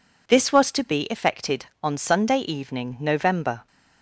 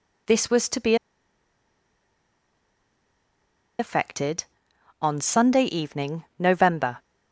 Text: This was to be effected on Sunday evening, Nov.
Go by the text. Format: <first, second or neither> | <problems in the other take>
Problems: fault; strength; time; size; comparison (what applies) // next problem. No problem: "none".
first | pauses between "be" and "effected"; strong; at 0.9 s; 2.8 s long